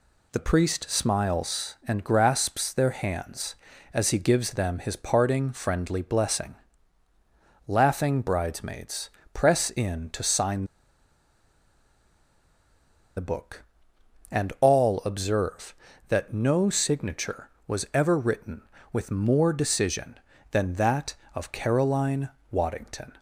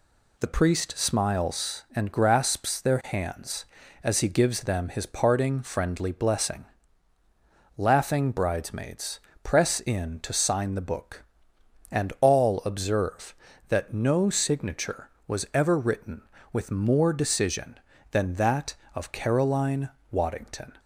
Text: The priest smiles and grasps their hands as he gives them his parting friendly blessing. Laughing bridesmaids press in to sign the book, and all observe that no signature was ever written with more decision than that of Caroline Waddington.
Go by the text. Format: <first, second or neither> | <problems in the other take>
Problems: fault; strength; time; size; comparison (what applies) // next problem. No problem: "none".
second | pauses between "bridesmaids" and "press"; slight; at 9.0 s; 0.24 s long; slight in the second // pauses between "sign" and "the"; strong; at 10.6 s; 2.5 s long // pauses between "Caroline" and "Waddington"; slight; at 22.2 s; 0.20 s long; slight in the second